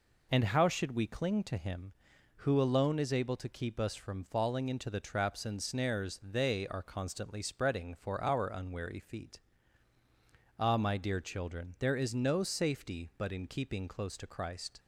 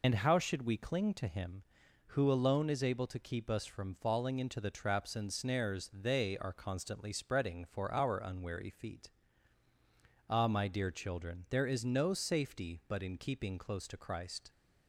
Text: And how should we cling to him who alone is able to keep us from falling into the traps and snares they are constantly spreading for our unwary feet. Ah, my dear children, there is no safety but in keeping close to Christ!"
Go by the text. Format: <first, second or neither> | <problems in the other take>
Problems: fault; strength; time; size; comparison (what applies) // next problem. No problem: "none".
first | loses the start of "And"; at 0.0 s; 30 ms